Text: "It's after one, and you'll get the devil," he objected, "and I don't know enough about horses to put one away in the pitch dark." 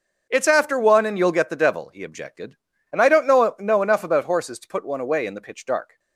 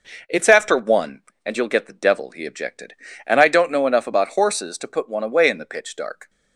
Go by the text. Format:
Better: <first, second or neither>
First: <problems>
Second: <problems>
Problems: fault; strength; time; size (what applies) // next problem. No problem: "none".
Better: second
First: starts louder than the rest; noticeable; until 1.2 s; 6 dB // says "know" twice; at 3.5 s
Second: none